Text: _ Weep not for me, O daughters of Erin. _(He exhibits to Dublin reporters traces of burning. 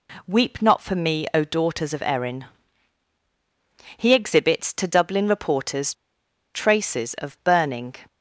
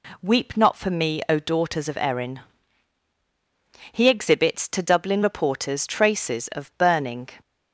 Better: second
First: pauses between "reporters" and "traces"; noticeable; at 5.9 s; 0.61 s long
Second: none

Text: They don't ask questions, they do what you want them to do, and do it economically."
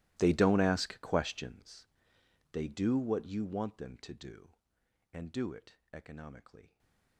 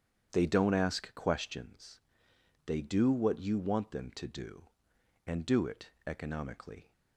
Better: second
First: gets quieter; strong; throughout; 23.5 dB // starts louder than the rest; strong; until 1.2 s; 17.5 dB // pauses between "it" and "economically"; slight; at 5.7 s; 0.16 s long // stays silent after the last word; slight; from 6.6 s on; 0.5 s long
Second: starts louder than the rest; strong; until 1.3 s; 8.5 dB // pauses between "it" and "economically"; slight; at 5.8 s; 0.16 s long

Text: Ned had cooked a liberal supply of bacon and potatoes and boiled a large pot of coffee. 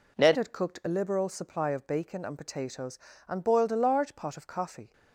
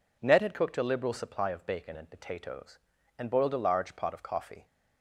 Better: second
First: changes voice at "had"; from 0.3 s on; 4.6 s long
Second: none

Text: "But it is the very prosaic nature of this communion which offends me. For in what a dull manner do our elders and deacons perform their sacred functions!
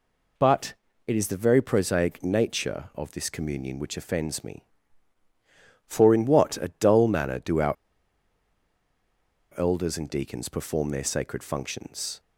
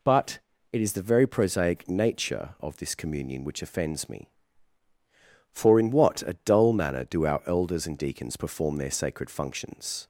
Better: second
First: pauses between "But" and "it"; slight; at 0.7 s; 0.34 s long // pauses between "our" and "elders"; strong; at 7.7 s; 1.8 s long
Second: pauses between "But" and "it"; slight; at 0.3 s; 0.34 s long

